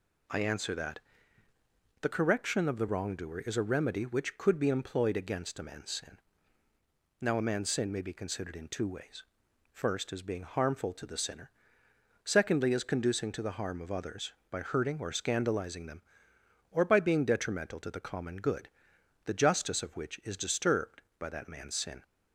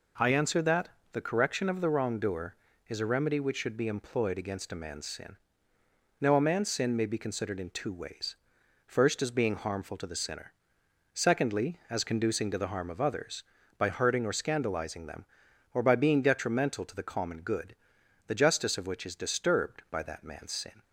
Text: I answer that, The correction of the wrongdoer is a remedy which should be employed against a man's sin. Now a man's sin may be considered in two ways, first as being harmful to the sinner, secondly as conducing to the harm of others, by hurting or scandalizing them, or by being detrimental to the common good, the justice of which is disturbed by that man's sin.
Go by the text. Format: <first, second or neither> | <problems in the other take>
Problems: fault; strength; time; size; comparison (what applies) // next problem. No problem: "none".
second | says "could" for "should"; at 4.3 s